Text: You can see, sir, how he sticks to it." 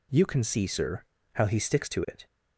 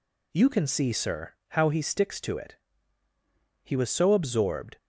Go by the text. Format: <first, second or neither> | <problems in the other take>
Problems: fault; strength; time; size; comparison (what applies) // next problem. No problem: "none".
first | goes on to say "He was so absorbed"; noticeable; from 3.6 s on; 1.1 s long